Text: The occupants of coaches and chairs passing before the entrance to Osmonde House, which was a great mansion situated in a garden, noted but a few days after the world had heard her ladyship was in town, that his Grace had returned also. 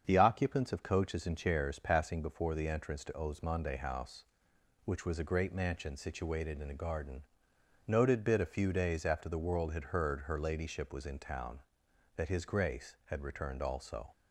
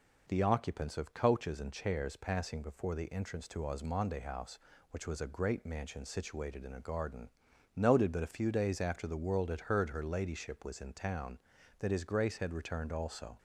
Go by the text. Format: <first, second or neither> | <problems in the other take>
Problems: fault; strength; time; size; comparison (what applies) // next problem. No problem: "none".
second | starts louder than the rest; strong; until 1.0 s; 7.5 dB // says "bit" for "but"; at 8.2 s